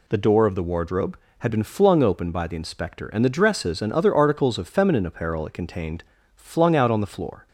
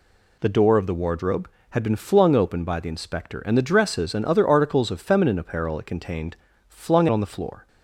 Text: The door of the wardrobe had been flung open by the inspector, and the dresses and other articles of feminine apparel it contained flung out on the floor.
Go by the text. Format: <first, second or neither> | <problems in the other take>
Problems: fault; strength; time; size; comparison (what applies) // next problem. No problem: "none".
first | pauses between "contained" and "flung"; slight; at 6.3 s; 0.32 s long; slight in the first // skips "out"; at 7.0 s